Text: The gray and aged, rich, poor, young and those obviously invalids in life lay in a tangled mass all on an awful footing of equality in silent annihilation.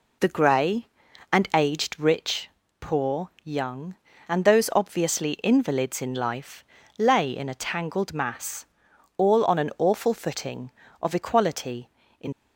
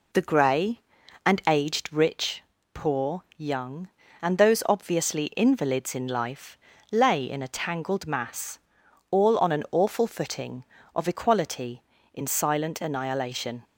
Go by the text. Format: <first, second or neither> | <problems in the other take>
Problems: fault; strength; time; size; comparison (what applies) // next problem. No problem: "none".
second | pauses between "life" and "lay"; slight; at 6.6 s; 0.34 s long; slight in the second // pauses between "mass" and "all"; noticeable; at 8.6 s; 0.52 s long; noticeable in the second // stops before "silent annihilation"; at 12.3 s